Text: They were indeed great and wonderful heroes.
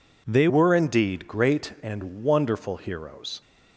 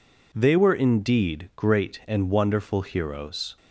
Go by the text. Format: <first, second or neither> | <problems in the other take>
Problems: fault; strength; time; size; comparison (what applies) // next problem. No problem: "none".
second | changes voice at "were"; from 0.4 s on; 3.0 s long